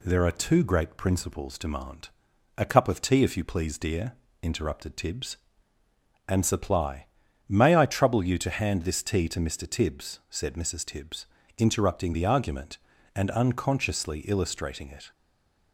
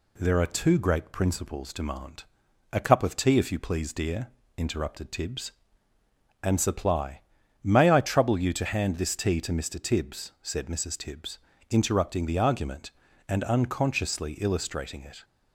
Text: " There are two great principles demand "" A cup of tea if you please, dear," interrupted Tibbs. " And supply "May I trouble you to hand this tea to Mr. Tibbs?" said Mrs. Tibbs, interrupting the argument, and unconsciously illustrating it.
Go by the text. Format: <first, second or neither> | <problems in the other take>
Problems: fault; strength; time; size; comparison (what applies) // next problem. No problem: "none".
second | pauses between "supply" and "May"; at 7.0 s; 0.42 s long; also in the second // stays silent after the last word; slight; from 15.1 s on; 0.6 s long